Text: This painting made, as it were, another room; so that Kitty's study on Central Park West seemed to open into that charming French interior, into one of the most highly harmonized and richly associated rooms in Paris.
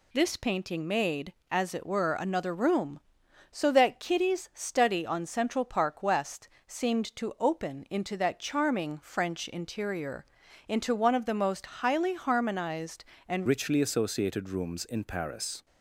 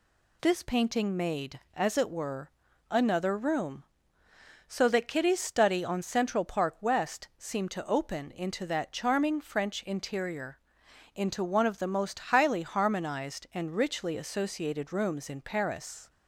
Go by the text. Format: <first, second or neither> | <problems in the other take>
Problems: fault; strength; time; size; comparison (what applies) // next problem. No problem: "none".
second | pauses between "West" and "seemed"; slight; at 6.4 s; 0.18 s long // changes voice at "richly"; from 13.4 s on; 2.2 s long